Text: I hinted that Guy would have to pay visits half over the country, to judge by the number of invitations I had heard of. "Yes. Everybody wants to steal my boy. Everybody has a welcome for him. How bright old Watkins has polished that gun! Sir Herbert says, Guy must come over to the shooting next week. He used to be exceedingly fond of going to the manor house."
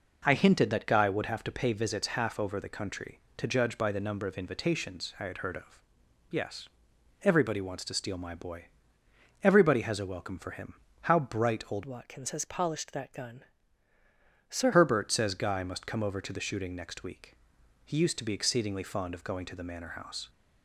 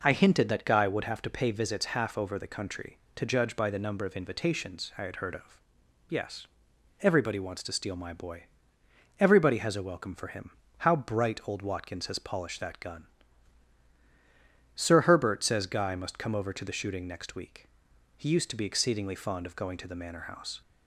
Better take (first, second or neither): second